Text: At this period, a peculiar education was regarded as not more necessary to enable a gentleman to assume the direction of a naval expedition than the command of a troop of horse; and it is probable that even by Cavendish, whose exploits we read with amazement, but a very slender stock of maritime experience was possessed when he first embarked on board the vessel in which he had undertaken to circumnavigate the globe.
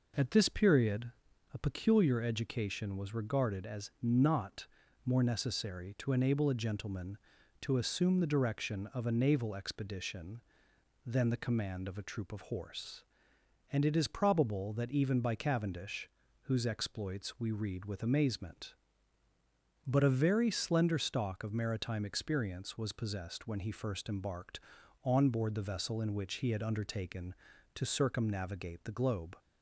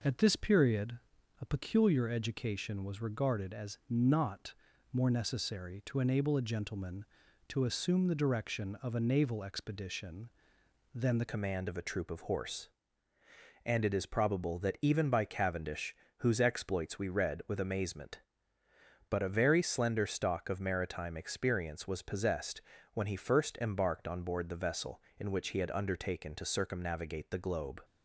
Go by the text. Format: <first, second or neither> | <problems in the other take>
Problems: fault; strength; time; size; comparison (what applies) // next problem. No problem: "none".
first | pauses between "not" and "more"; at 4.5 s; 0.38 s long; also in the first // changes voice at "command"; from 11.2 s on; 16.6 s long // pauses between "possessed" and "when"; slight; at 22.6 s; 0.34 s long